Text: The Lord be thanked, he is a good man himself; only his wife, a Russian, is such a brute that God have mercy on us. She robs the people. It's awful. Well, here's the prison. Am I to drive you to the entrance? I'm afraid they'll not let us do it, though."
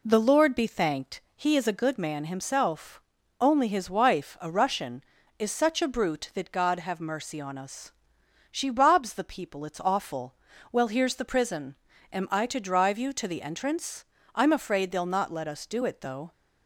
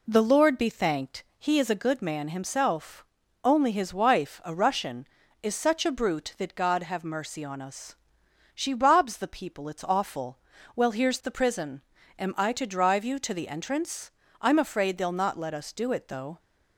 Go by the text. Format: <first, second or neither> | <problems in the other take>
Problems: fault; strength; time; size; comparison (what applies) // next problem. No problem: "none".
neither | none